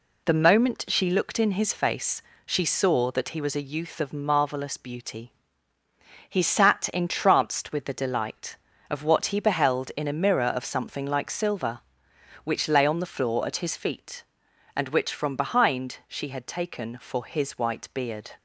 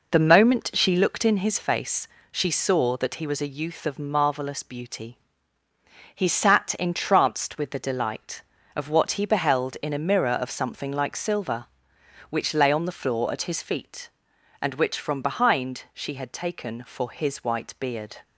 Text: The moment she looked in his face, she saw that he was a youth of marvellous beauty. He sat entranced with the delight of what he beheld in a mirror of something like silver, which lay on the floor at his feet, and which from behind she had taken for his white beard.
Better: first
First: none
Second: starts louder than the rest; noticeable; until 1.4 s; 4.5 dB

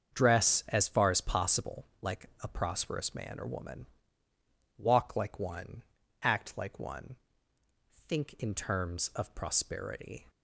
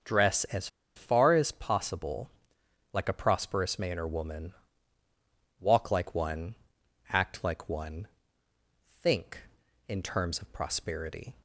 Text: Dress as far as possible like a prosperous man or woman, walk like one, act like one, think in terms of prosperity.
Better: first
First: starts louder than the rest; until 1.2 s; 7 dB // pauses between "possible" and "like"; slight; at 1.8 s; 0.16 s long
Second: starts louder than the rest; until 1.3 s; 6.5 dB // pauses between "as" and "far"; slight; at 0.6 s; 0.29 s long // pauses between "possible" and "like"; noticeable; at 2.2 s; 0.64 s long

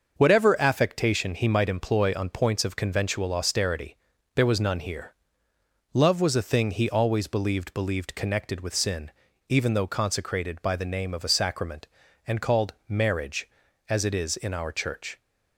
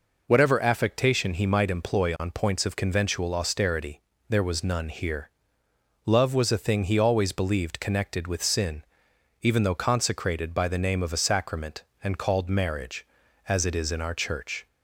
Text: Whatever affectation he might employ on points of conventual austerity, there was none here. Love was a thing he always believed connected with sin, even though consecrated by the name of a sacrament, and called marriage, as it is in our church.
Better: second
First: starts louder than the rest; until 1.1 s; 6.5 dB // says "believed" twice; at 7.7 s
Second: none

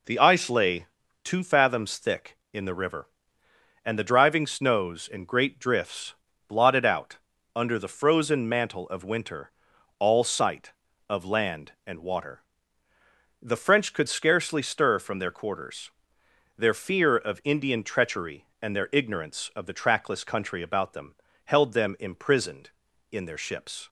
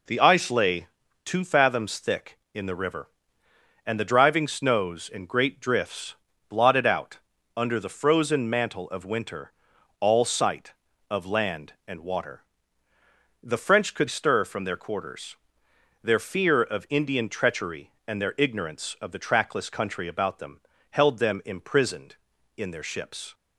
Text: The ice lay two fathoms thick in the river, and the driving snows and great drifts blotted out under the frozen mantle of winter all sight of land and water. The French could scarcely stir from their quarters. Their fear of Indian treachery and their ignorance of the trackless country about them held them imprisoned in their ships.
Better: first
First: pauses between "lay" and "two"; at 0.8 s; 0.38 s long // pauses between "drifts" and "blotted"; slight; at 6.1 s; 0.34 s long // pauses between "out" and "under"; at 7.1 s; 0.38 s long // pauses between "winter" and "all"; noticeable; at 9.4 s; 0.48 s long // pauses between "them" and "held"; slight; at 21.1 s; 0.30 s long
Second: pauses between "lay" and "two"; at 0.8 s; 0.38 s long // pauses between "drifts" and "blotted"; slight; at 6.1 s; 0.34 s long // pauses between "out" and "under"; at 7.1 s; 0.38 s long // pauses between "winter" and "all"; noticeable; at 9.5 s; 0.48 s long // skips "scarcely"; at 14.0 s // pauses between "them" and "held"; slight; at 20.5 s; 0.30 s long

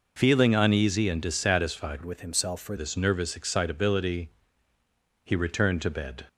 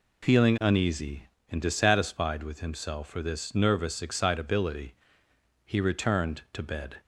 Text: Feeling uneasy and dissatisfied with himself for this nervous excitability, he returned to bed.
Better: second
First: changes voice from "with" to "for"; from 2.0 to 2.7 s; 0.7 s long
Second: none

